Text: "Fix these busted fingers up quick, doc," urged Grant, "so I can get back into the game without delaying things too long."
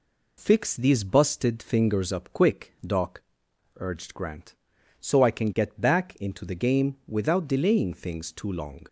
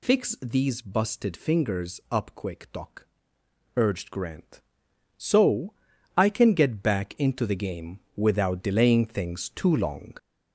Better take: first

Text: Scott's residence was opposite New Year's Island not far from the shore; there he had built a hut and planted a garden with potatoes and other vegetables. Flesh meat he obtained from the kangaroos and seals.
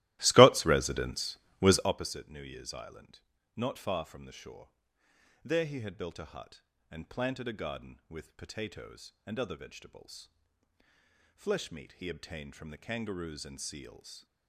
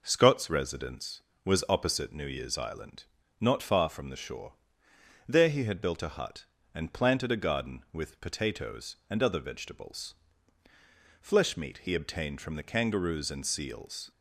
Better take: second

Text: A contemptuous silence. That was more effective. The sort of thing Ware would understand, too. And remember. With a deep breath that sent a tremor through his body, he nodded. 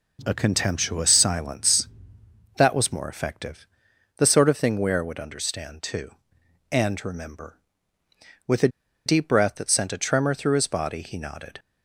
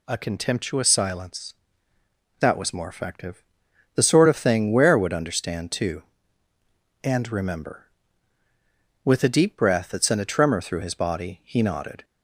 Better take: second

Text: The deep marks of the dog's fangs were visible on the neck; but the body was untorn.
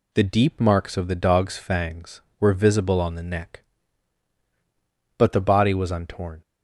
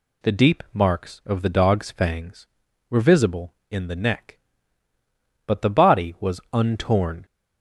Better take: first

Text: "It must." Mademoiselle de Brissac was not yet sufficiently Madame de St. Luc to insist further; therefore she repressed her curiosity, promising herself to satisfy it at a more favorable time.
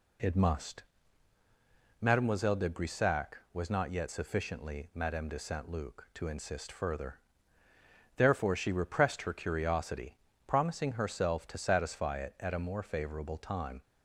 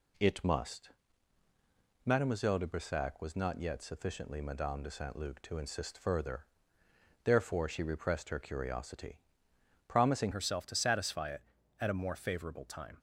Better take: first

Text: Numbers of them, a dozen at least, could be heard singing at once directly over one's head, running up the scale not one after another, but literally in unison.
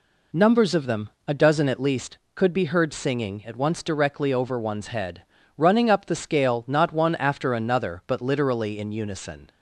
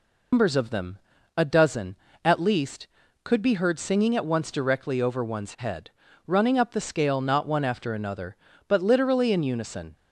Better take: first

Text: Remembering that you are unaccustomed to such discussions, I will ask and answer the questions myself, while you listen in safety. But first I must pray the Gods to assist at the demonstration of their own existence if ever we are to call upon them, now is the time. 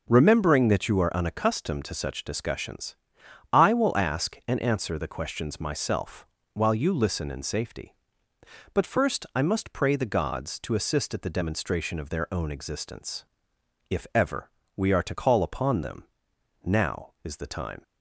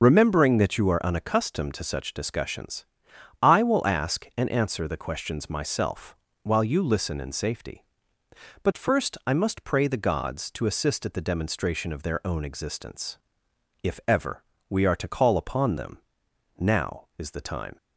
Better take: first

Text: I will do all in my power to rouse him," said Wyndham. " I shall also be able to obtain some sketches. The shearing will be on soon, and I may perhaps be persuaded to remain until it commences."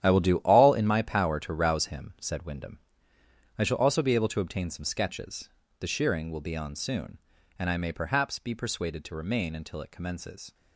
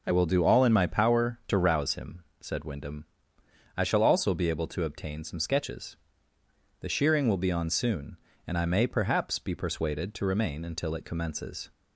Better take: second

